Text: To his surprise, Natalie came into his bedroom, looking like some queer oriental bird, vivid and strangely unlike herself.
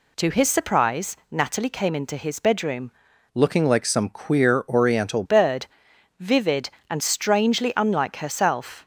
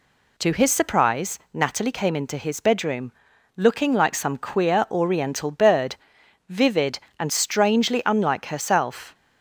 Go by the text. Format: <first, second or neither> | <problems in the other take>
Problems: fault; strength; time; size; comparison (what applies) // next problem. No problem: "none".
second | changes voice from "looking" to "oriental"; from 3.3 to 5.2 s; 1.9 s long